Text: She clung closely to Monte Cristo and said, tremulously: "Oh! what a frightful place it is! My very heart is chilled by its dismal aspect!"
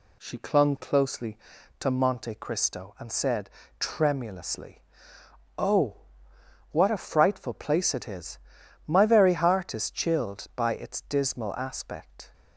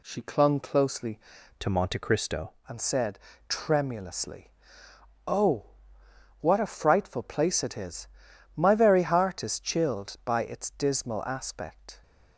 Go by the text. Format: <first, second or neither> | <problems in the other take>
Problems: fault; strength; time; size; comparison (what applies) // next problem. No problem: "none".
first | changes voice from "to" to "Cristo"; from 1.5 to 2.5 s; 1.0 s long